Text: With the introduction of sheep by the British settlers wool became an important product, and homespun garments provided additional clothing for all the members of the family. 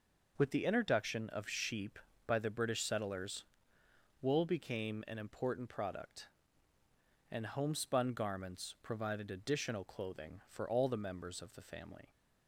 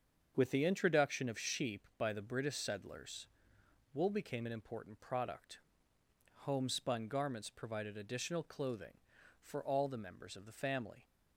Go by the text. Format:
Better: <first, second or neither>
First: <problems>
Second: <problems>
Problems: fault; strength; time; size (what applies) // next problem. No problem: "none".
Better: first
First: pauses between "settlers" and "wool"; noticeable; at 3.4 s; 0.74 s long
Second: starts louder than the rest; until 1.3 s; 7 dB // pauses between "settlers" and "wool"; noticeable; at 3.2 s; 0.68 s long // skips "and"; at 5.9 s